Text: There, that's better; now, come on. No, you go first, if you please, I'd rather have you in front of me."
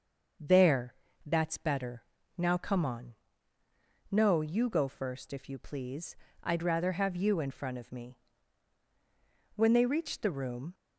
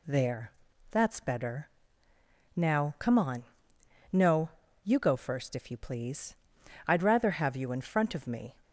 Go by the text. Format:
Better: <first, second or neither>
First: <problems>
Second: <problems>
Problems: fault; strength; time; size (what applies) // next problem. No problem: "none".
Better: second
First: starts louder than the rest; until 1.7 s; 6.5 dB // goes on to say "When they reached the room"; noticeable; from 9.5 s on; 1.1 s long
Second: none